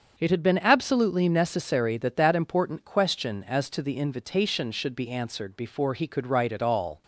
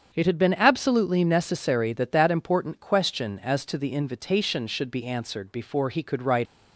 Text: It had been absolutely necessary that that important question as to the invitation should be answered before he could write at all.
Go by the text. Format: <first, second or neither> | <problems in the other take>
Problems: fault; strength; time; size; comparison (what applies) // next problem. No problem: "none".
first | starts louder than the rest; strong; until 1.1 s; 7.5 dB; also in the first // stops before "at all"; at 6.4 s